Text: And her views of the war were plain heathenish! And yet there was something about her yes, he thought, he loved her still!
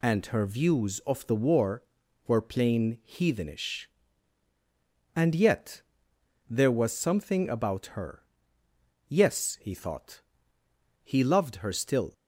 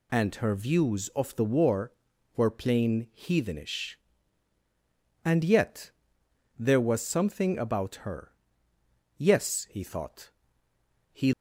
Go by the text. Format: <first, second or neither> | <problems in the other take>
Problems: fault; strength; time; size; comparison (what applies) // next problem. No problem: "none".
first | pauses between "yet" and "there"; noticeable; at 5.8 s; 0.68 s long; noticeable in the first // pauses between "her" and "yes"; noticeable; at 8.3 s; 0.86 s long; noticeable in the first // stops before "loved her still"; at 11.3 s